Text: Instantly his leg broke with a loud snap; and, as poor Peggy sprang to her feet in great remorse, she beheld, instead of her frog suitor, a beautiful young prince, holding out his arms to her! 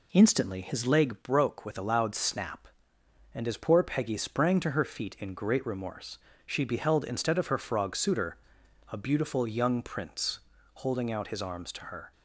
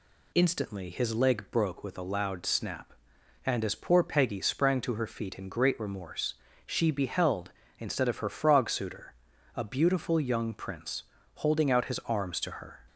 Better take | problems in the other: second | starts louder than the rest; slight; until 1.0 s; 2.5 dB

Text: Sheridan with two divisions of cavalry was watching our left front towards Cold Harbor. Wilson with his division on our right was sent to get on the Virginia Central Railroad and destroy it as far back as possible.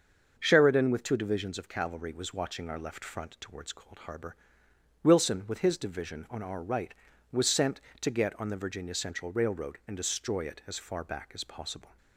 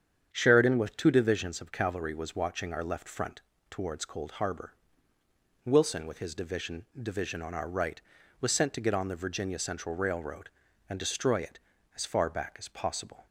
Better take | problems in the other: first | starts louder than the rest; strong; until 1.3 s; 8 dB; also in the first // pauses between "front" and "towards"; slight; at 3.4 s; 0.28 s long // says "division" twice; at 6.9 s

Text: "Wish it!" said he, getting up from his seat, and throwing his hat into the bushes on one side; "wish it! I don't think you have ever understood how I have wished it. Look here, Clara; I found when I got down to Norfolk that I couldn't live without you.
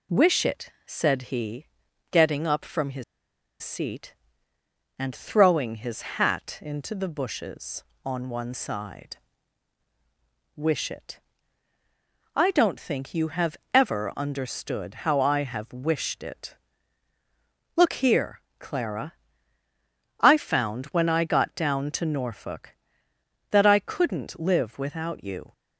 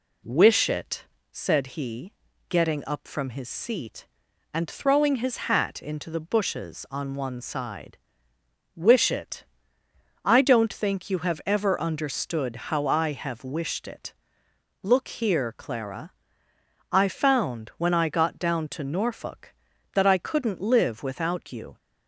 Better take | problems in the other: second | pauses between "his" and "seat"; noticeable; at 3.0 s; 0.58 s long // pauses between "his" and "hat"; slight; at 6.0 s; 0.18 s long // pauses between "have" and "ever"; slight; at 13.5 s; 0.16 s long

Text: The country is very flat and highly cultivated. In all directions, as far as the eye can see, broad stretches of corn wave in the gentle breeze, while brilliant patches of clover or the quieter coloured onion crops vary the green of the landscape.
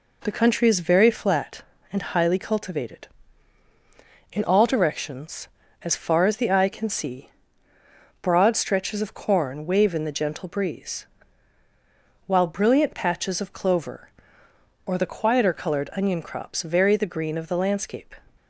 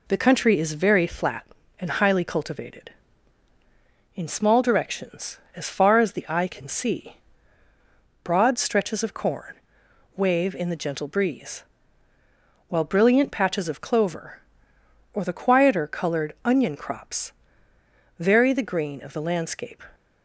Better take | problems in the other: first | says "small" for "all"; at 4.2 s // pauses between "corn" and "wave"; noticeable; at 9.5 s; 0.60 s long // pauses between "crops" and "vary"; noticeable; at 17.3 s; 0.86 s long

